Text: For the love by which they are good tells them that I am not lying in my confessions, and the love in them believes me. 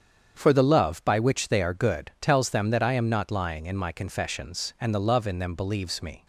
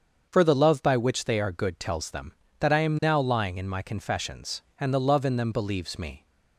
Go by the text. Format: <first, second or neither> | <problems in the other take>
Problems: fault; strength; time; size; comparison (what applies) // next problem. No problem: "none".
first | starts louder than the rest; strong; until 1.3 s; 7 dB; strong in the first // says "now" for "not"; at 3.0 s